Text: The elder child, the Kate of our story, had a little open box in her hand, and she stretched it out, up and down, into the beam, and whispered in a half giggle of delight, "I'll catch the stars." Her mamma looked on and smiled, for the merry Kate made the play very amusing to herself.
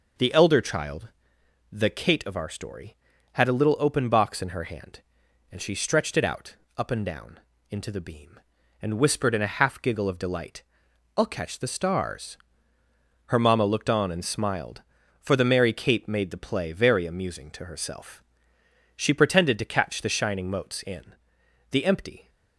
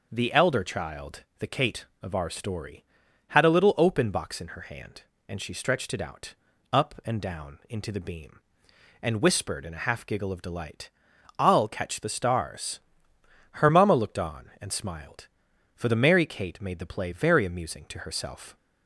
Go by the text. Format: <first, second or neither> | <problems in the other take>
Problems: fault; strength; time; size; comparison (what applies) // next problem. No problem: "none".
second | goes on to say "She pretended to catch the shining motes in the empty"; strong; from 18.9 s on; 3.3 s long